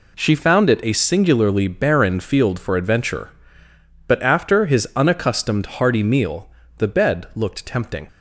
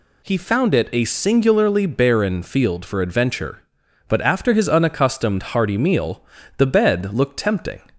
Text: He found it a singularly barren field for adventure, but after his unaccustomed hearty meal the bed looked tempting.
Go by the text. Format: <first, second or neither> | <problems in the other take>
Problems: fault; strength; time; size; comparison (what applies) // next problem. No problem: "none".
second | says "She" for "He"; at 0.1 s // pauses between "meal" and "the"; slight; at 6.4 s; 0.30 s long; slight in the second